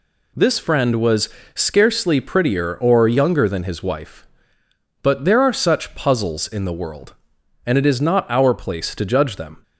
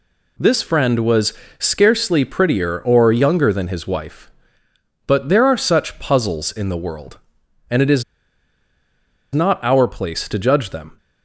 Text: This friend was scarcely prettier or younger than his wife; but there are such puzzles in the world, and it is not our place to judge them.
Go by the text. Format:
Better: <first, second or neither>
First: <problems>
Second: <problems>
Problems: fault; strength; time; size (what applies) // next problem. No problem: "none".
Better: first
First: pauses between "was" and "scarcely"; slight; at 1.2 s; 0.24 s long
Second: pauses between "was" and "scarcely"; slight; at 1.3 s; 0.24 s long // pauses between "is" and "not"; strong; at 8.0 s; 1.3 s long